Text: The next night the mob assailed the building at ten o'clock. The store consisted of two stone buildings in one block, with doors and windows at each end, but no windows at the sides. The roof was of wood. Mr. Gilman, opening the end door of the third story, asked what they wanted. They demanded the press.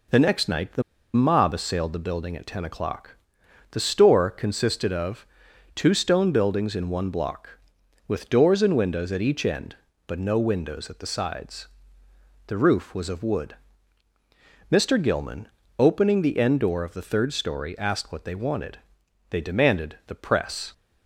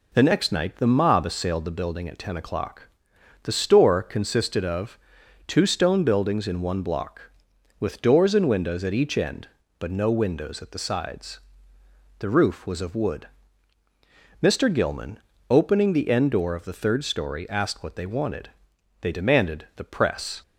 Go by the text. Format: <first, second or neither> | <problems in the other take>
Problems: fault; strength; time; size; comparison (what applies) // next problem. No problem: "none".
second | pauses between "the" and "mob"; slight; at 0.8 s; 0.32 s long // pauses between "of" and "two"; noticeable; at 5.2 s; 0.48 s long; noticeable in the second